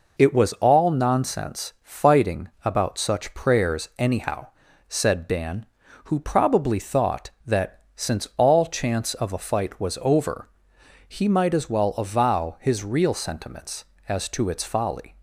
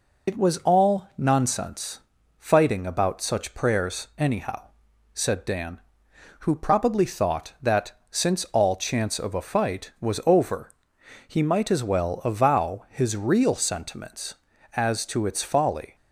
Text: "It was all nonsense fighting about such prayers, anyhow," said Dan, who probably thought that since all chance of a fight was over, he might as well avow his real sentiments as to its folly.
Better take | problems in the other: first | loses the start of "It"; at 0.2 s; 65 ms // pauses between "nonsense" and "fighting"; slight; at 2.0 s; 0.36 s long // pauses between "that" and "since"; slight; at 7.9 s; 0.18 s long

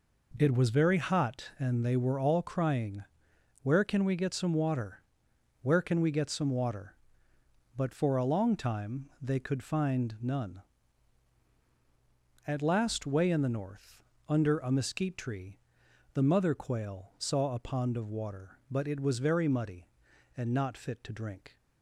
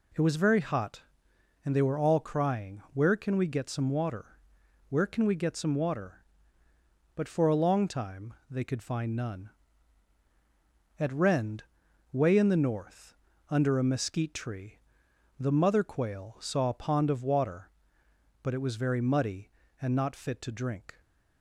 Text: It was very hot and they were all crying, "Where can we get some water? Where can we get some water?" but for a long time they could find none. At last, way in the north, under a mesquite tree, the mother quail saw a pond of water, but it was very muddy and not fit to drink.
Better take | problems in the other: first | pauses between "time" and "they"; slight; at 8.3 s; 0.16 s long // says "rend" for "last"; at 11.1 s

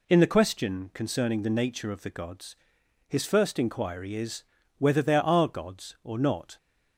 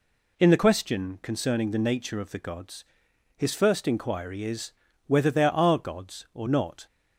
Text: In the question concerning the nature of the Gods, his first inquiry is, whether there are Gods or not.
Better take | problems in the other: neither | none

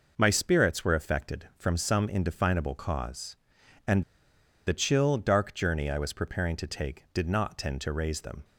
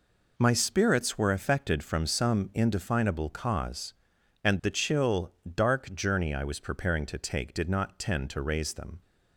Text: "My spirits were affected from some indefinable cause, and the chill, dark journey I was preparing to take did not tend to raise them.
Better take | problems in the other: second | pauses between "and" and "the"; noticeable; at 4.0 s; 0.63 s long

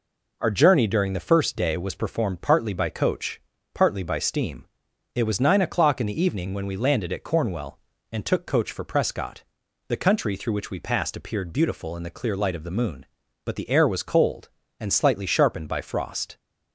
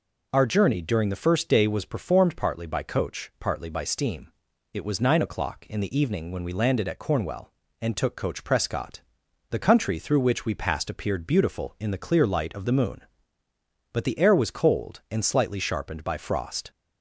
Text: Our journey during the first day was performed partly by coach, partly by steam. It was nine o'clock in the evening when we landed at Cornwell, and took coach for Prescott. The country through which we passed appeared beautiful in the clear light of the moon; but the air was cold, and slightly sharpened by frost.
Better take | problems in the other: first | skips "for"; at 8.4 s

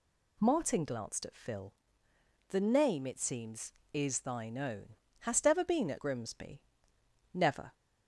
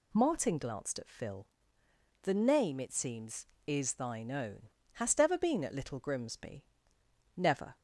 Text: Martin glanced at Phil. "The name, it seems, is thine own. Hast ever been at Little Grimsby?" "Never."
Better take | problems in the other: second | skips "Little"; at 5.9 s

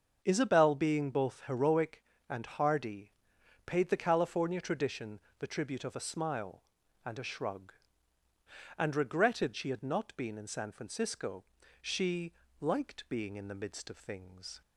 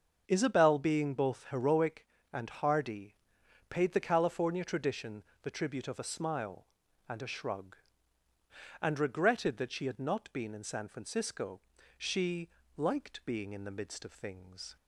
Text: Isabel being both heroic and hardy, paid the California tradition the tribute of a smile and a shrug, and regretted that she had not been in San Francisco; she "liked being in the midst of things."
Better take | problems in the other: second | starts louder than the rest; until 1.2 s; 6.5 dB; also in the second // pauses between "tradition" and "the"; slight; at 5.1 s; 0.18 s long; slight in the second // skips "that"; at 9.5 s // pauses between "she" and "liked"; slight; at 12.3 s; 0.28 s long; slight in the second

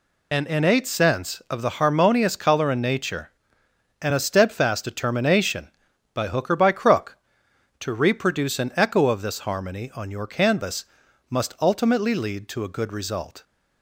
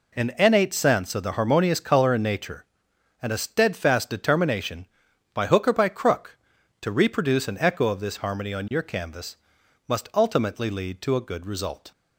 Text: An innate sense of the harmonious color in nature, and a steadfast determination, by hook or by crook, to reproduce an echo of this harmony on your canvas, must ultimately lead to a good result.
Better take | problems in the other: second | loses the start of "An"; at 0.3 s; 30 ms

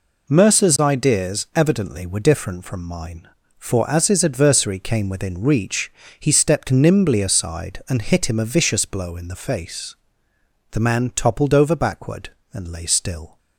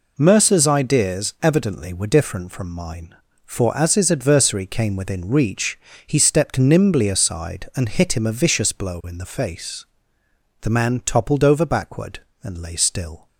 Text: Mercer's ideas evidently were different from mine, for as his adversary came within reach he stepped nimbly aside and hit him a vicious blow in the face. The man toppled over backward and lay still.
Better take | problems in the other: neither | pauses between "reach" and "he"; slight; the same in both

